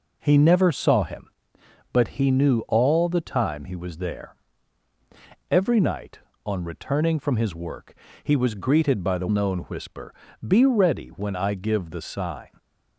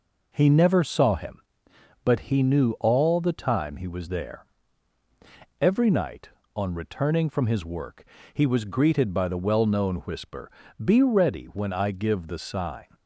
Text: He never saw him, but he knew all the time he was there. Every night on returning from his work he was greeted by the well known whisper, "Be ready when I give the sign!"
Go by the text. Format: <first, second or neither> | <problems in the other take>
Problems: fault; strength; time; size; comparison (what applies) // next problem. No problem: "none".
second | pauses between "work" and "he"; slight; at 7.9 s; 0.30 s long; slight in the second // skips "well"; at 9.2 s